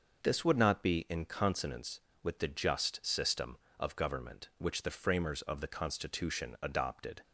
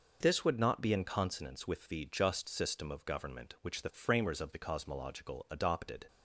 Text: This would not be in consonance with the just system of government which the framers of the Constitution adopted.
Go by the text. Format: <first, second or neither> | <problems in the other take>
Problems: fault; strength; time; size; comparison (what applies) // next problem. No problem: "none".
first | says "Cosmological" for "Constitution"; at 4.5 s